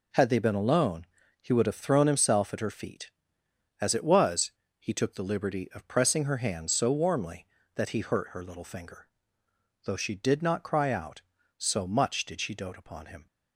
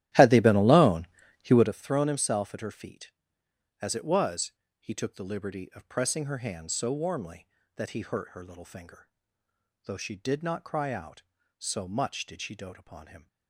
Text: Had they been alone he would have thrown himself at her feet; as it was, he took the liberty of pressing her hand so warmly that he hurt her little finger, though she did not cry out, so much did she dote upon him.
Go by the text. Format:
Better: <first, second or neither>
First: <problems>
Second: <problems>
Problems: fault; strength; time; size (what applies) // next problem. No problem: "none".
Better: first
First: pauses between "alone" and "he"; at 1.0 s; 0.38 s long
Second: starts louder than the rest; strong; until 1.7 s; 14 dB // pauses between "alone" and "he"; at 1.0 s; 0.38 s long